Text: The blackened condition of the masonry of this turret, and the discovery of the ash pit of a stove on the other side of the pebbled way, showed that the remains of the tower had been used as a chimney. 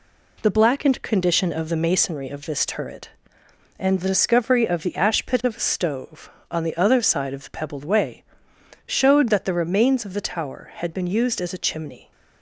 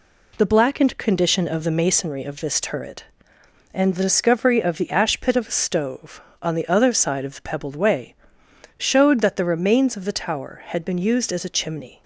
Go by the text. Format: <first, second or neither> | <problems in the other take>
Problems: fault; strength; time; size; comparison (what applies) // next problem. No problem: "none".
neither | none